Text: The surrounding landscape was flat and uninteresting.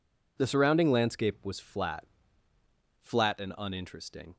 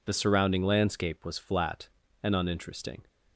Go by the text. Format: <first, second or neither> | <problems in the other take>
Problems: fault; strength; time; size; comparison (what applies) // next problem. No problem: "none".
second | says "flat" twice; at 2.9 s